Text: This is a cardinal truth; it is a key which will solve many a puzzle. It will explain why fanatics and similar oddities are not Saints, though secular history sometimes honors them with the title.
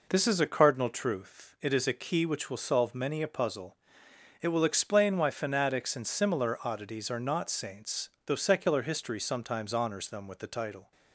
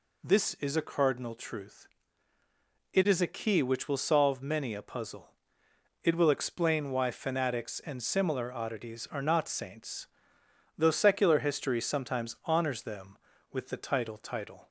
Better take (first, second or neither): first